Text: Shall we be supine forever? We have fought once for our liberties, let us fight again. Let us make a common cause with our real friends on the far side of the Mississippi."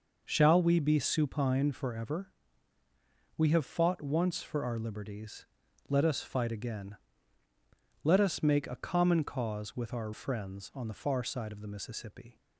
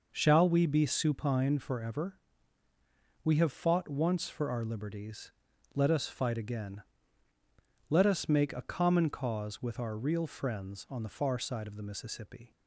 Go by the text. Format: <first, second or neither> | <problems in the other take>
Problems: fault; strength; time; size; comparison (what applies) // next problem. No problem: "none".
second | skips "real"; at 10.1 s